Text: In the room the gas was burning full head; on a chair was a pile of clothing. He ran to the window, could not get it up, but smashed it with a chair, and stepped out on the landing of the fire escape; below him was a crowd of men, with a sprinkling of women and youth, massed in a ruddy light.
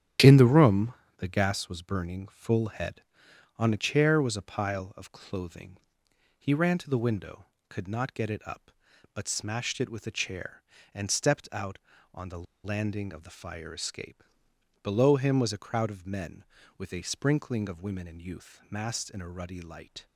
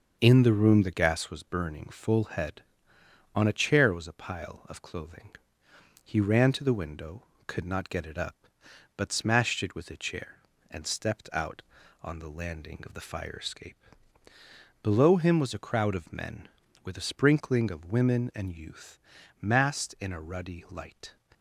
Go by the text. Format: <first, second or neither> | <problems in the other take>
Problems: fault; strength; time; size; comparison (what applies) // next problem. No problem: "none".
second | starts louder than the rest; strong; until 1.4 s; 9.5 dB; also in the second // pauses between "room" and "the"; slight; at 0.9 s; 0.24 s long // pauses between "the" and "landing"; slight; at 12.4 s; 0.21 s long